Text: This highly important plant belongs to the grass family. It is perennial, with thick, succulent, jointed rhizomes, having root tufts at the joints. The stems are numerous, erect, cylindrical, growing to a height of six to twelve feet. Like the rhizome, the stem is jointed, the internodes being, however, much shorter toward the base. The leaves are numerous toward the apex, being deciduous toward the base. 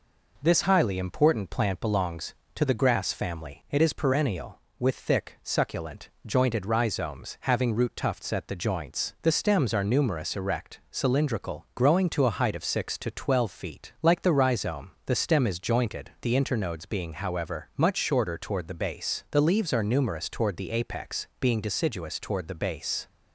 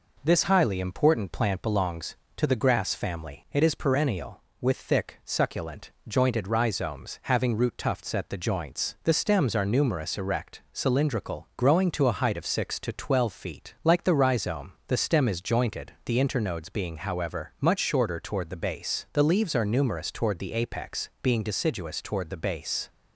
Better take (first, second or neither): neither